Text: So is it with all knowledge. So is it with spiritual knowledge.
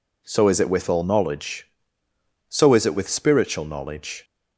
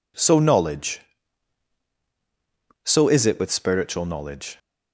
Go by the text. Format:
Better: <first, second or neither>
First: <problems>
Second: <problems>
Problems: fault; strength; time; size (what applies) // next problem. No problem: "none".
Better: first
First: none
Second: skips "is it with all"; at 0.3 s